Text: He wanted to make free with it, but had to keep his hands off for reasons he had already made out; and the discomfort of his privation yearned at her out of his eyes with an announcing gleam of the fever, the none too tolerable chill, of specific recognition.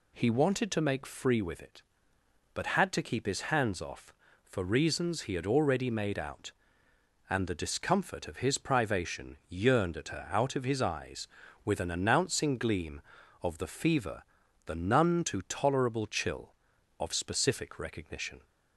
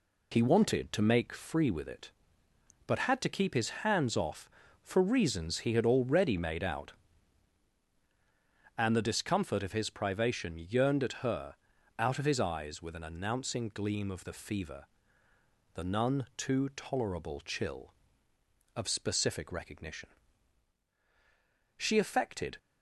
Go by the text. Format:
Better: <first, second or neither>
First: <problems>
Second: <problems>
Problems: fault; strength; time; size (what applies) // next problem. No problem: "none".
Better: first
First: none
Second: pauses between "his" and "hands"; slight; at 3.6 s; 0.16 s long // pauses between "her" and "out"; at 11.5 s; 0.42 s long // goes on to say "She affected"; noticeable; from 21.7 s on; 0.80 s long